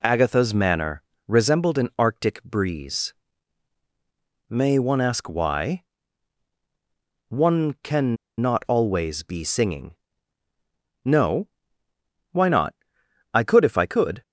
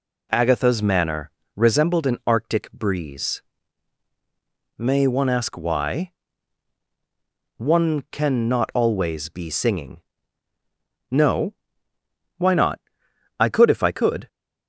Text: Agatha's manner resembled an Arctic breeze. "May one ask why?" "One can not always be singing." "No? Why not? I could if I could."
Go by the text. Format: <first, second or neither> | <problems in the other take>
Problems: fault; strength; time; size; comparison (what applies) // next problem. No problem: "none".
second | pauses between "manner" and "resembled"; slight; at 1.0 s; 0.24 s long; slight in the second // pauses between "can" and "not"; slight; at 8.1 s; 0.23 s long